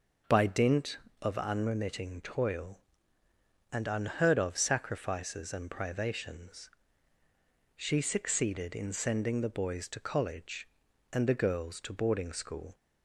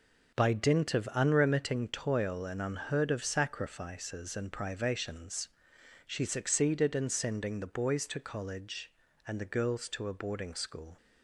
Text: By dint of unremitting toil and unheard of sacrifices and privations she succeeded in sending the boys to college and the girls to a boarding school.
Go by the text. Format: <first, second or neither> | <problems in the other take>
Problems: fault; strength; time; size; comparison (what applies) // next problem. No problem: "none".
second | pauses between "privations" and "she"; at 6.6 s; 1.0 s long; noticeable in the second // skips "a"; at 11.9 s